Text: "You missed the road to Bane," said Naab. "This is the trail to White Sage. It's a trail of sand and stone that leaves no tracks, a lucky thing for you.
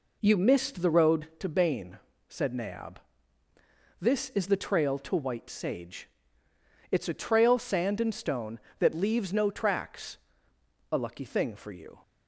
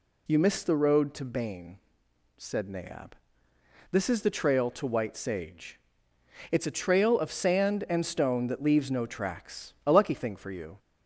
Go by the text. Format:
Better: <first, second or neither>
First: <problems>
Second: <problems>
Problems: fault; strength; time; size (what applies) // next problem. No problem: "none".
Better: second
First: skips "of"; at 7.5 s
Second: none